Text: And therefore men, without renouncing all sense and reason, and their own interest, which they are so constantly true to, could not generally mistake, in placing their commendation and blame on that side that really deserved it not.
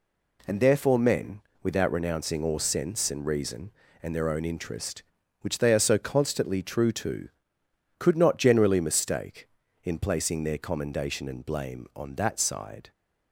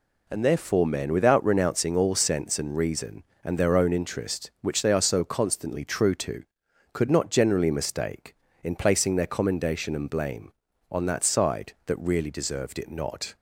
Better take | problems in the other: second | stops before "that really deserved it not"; at 12.9 s

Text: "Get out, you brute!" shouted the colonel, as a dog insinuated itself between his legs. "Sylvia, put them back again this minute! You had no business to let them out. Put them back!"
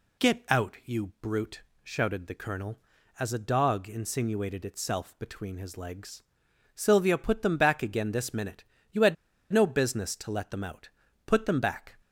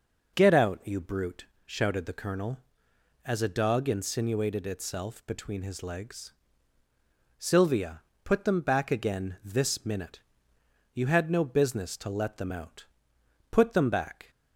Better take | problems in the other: second | pauses between "had" and "no"; at 9.1 s; 0.37 s long

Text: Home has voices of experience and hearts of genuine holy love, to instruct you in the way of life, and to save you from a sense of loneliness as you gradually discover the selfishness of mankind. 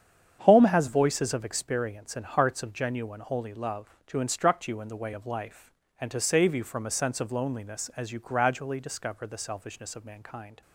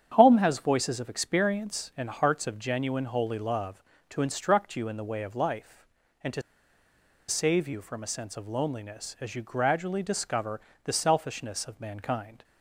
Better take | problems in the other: first | starts louder than the rest; strong; until 1.1 s; 8.5 dB; strong in the first // pauses between "to" and "save"; noticeable; at 6.4 s; 0.87 s long // pauses between "discover" and "the"; slight; at 10.5 s; 0.24 s long

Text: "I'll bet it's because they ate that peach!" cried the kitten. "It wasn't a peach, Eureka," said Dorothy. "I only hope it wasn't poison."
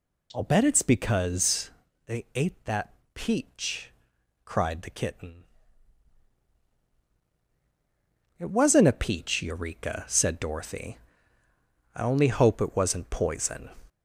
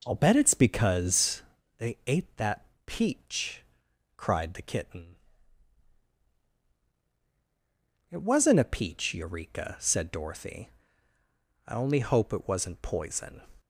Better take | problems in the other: second | gets louder; slight; throughout; 3 dB // pauses between "because" and "they"; slight; at 1.7 s; 0.34 s long; slight in the second // pauses between "that" and "peach"; slight; at 2.9 s; 0.22 s long; slight in the second

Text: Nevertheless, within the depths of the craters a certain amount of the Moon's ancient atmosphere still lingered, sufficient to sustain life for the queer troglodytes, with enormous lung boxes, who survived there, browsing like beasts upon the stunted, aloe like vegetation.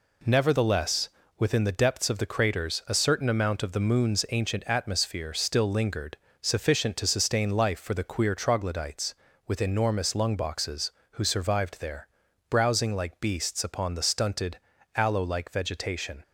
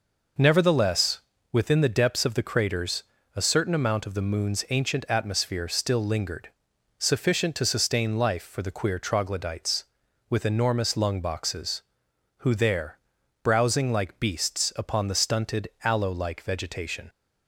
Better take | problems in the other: first | pauses between "craters" and "a"; slight; at 3.0 s; 0.32 s long // skips "survived"; at 12.5 s

